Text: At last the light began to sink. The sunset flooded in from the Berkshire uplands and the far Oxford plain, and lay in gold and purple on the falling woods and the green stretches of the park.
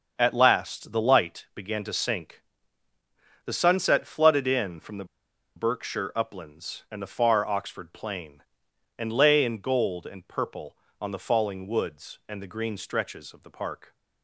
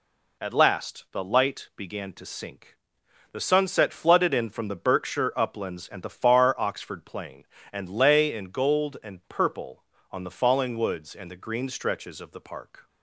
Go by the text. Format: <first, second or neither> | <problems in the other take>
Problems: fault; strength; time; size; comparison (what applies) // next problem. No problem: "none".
second | starts louder than the rest; until 1.1 s; 6.5 dB // pauses between "the" and "Berkshire"; noticeable; at 5.0 s; 0.51 s long